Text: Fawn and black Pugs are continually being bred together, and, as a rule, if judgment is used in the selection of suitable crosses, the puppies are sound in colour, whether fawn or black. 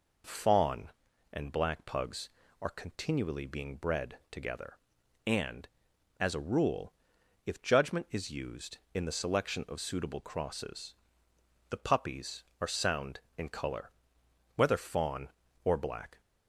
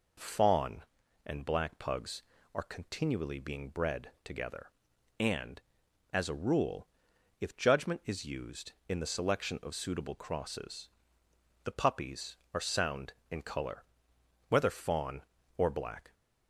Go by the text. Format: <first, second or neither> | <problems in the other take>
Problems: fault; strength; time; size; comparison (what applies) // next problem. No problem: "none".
neither | none